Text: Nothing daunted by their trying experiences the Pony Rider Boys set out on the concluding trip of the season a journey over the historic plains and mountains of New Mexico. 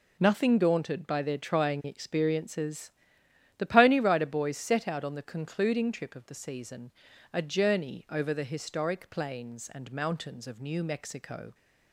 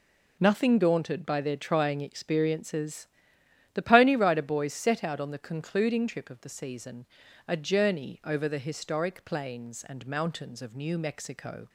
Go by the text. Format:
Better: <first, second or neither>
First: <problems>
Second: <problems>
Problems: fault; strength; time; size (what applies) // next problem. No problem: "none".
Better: neither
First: pauses between "experiences" and "the"; noticeable; at 2.9 s; 0.68 s long // pauses between "season" and "a"; at 6.9 s; 0.40 s long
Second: pauses between "experiences" and "the"; noticeable; at 3.0 s; 0.68 s long // pauses between "season" and "a"; at 7.0 s; 0.40 s long